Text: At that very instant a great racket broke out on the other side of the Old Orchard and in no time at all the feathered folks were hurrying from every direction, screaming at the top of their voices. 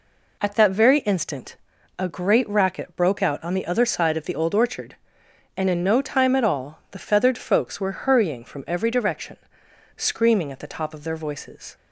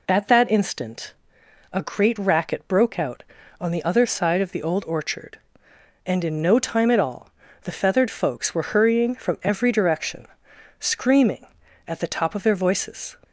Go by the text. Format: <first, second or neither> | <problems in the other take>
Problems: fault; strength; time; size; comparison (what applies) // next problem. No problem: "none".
first | skips "very"; at 0.5 s // pauses between "instant" and "a"; noticeable; at 1.1 s; 0.58 s long; also in the first // pauses between "all" and "the"; slight; at 7.3 s; 0.32 s long